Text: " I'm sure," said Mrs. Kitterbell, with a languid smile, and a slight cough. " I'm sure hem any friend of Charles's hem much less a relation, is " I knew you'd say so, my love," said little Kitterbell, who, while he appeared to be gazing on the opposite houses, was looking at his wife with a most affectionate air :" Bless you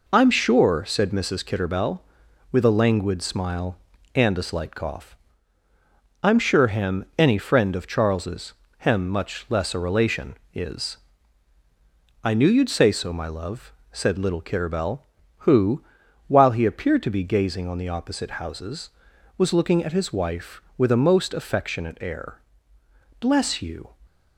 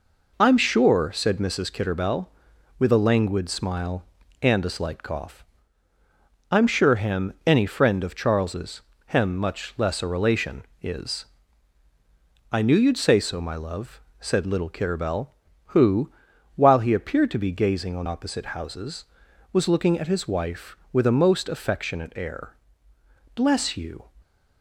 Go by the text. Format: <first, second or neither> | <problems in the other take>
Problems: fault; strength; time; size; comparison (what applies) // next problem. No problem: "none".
first | pauses between "Charles's" and "hem"; slight; at 8.8 s; 0.24 s long; slight in the first // skips "the"; at 18.0 s